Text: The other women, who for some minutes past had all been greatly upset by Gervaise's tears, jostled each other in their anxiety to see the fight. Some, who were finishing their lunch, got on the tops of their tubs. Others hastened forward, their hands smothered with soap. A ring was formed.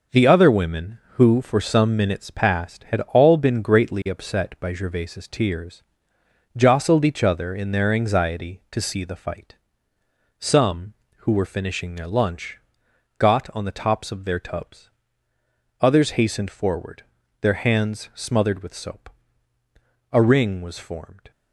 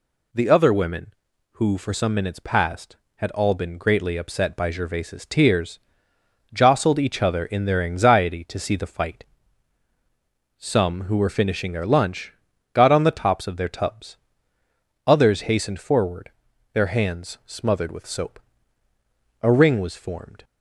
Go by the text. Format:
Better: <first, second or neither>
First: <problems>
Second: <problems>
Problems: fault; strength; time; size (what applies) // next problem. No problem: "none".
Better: second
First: gets quieter; strong; throughout; 7 dB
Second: none